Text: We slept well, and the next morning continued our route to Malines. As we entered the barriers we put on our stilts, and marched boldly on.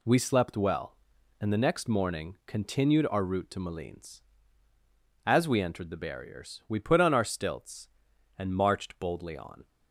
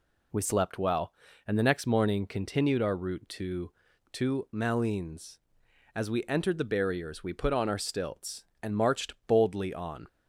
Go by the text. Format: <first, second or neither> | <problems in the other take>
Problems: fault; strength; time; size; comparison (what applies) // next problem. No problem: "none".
first | says "to" twice; at 4.1 s